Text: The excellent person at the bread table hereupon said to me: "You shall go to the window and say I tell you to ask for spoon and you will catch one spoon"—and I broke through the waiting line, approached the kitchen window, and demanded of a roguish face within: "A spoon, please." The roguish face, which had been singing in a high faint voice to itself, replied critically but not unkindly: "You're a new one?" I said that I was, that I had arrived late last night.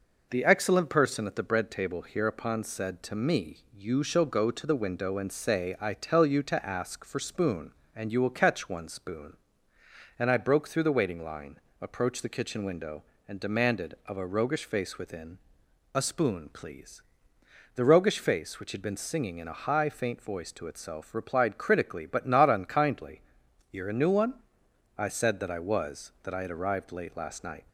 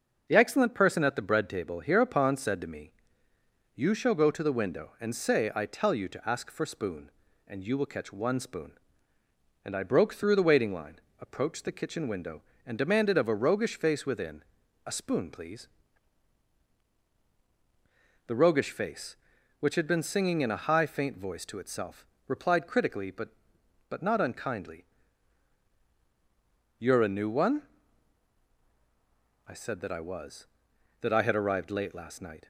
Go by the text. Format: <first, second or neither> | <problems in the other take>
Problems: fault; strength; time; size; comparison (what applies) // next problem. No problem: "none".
first | starts louder than the rest; until 1.2 s; 6.5 dB // says "but" twice; at 23.8 s